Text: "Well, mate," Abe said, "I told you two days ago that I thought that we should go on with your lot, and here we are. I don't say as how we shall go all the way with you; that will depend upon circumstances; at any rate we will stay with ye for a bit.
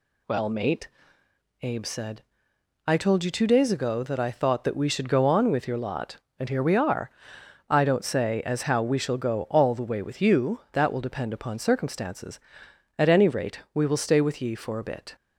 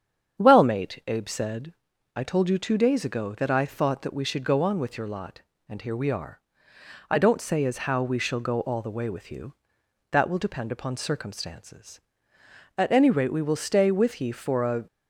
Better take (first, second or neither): first